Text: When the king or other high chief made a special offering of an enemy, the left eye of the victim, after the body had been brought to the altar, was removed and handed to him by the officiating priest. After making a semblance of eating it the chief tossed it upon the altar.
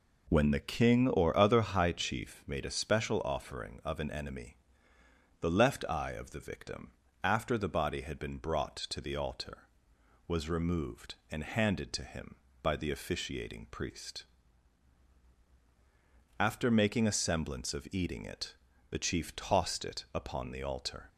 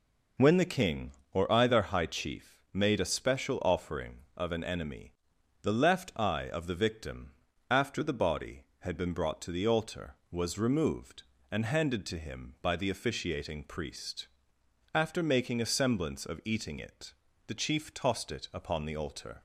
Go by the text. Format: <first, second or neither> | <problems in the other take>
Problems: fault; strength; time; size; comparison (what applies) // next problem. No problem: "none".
first | says "either" for "other"; at 1.5 s // pauses between "it" and "the"; slight; at 17.1 s; 0.34 s long; slight in the first